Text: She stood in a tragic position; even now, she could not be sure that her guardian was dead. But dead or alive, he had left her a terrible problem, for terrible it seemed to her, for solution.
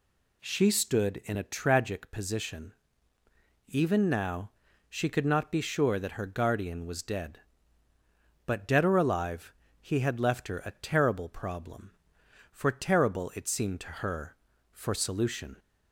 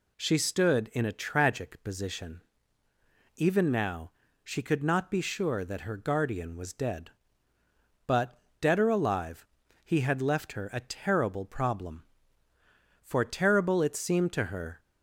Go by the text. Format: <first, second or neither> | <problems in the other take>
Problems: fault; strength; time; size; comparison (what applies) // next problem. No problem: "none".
first | pauses between "But" and "dead"; slight; at 8.3 s; 0.20 s long // stops before "for solution"; at 14.7 s